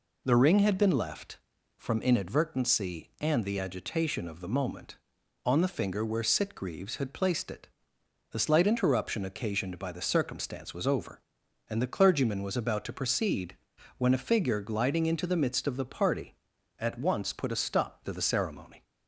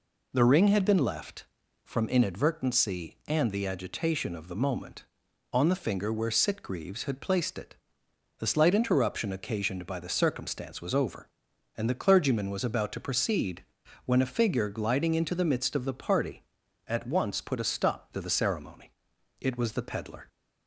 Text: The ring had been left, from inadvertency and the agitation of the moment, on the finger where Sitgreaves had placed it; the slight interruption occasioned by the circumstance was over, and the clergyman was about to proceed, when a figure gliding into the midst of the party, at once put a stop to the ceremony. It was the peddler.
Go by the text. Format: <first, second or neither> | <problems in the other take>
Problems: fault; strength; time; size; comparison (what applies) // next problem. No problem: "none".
second | stops before "It was the peddler"; at 18.8 s